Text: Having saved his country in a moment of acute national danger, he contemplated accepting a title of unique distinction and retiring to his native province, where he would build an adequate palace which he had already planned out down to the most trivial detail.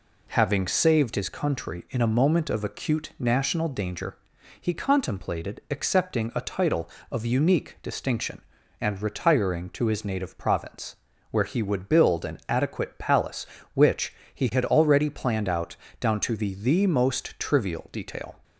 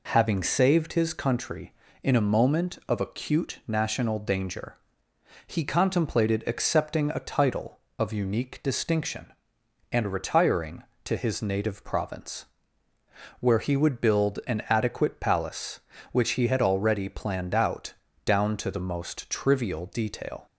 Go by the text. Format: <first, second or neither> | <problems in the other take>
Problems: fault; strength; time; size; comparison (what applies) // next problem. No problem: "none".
second | pauses between "which" and "he"; slight; at 14.1 s; 0.20 s long // pauses between "out" and "down"; slight; at 15.7 s; 0.24 s long; slight in the second // says "the" twice; at 16.5 s